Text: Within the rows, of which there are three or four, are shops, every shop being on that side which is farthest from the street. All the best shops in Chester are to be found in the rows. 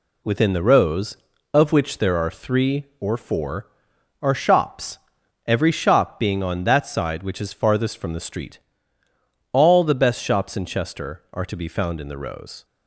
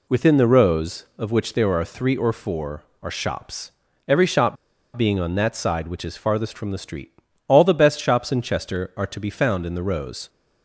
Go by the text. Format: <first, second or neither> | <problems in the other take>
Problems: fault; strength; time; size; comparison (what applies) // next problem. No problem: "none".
first | pauses between "shop" and "being"; at 4.5 s; 0.40 s long